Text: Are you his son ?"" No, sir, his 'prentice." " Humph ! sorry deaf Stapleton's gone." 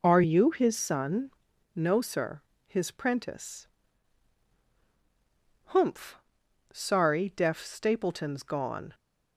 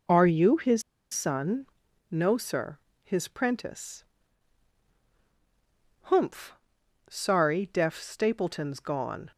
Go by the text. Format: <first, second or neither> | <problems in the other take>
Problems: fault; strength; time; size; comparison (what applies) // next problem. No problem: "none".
first | pauses between "his" and "son"; slight; at 0.8 s; 0.31 s long